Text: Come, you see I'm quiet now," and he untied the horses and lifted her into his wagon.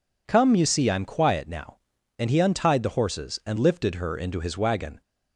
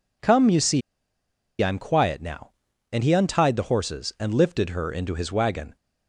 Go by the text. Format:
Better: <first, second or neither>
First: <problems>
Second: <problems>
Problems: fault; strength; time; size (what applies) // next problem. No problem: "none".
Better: first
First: none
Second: pauses between "see" and "I'm"; noticeable; at 0.8 s; 0.80 s long